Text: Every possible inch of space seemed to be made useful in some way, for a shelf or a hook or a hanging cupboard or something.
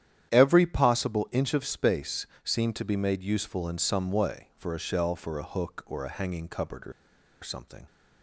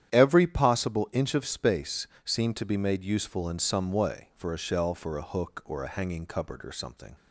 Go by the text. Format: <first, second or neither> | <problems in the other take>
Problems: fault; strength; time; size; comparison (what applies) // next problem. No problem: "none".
second | starts louder than the rest; strong; until 1.3 s; 10 dB; strong in the second // pauses between "space" and "seemed"; slight; at 2.2 s; 0.18 s long; slight in the second // pauses between "or" and "something"; noticeable; at 6.9 s; 0.51 s long